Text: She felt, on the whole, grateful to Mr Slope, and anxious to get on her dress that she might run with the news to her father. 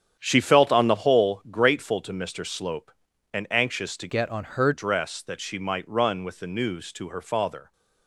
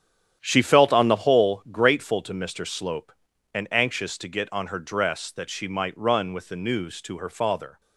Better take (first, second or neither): second